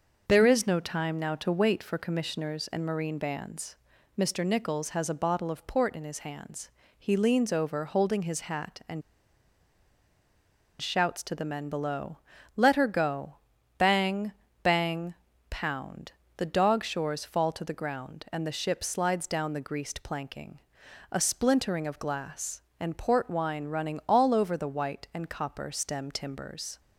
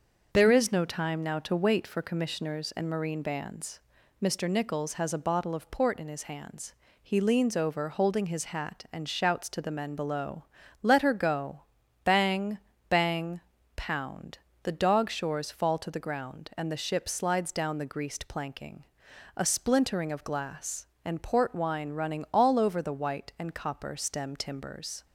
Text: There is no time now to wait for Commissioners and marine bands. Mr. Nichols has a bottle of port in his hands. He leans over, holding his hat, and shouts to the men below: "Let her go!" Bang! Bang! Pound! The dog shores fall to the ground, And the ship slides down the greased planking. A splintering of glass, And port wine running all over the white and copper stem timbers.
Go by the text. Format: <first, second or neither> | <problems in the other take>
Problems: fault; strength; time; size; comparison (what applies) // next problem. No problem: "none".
second | starts louder than the rest; until 1.2 s; 6.5 dB; also in the second // pauses between "and" and "shouts"; strong; at 9.0 s; 1.8 s long